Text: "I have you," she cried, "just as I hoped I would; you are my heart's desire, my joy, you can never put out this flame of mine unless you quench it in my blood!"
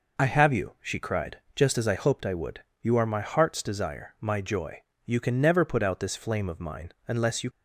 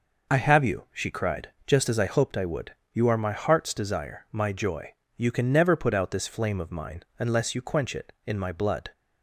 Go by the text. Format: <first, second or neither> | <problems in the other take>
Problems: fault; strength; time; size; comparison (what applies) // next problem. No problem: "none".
second | pauses between "mine" and "unless"; slight; at 6.9 s; 0.16 s long; slight in the second // stops before "quench it in my blood"; at 7.5 s